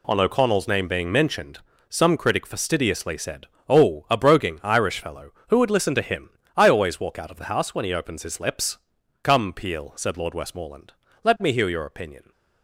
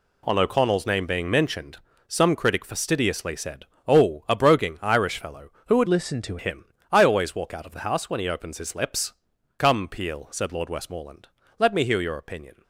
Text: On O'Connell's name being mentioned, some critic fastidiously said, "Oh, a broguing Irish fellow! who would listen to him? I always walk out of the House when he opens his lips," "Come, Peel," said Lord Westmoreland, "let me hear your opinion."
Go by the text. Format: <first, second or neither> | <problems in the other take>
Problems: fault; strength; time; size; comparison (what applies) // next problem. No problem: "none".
first | changes voice from "listen" to "to"; from 5.8 to 6.3 s; 0.5 s long